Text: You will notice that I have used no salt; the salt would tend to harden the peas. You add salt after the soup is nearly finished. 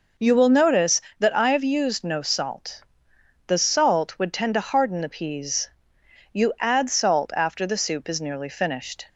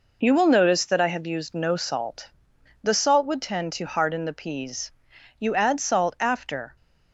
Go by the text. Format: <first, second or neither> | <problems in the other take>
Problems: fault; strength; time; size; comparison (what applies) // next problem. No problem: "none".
first | stops before "the soup is nearly finished"; at 6.7 s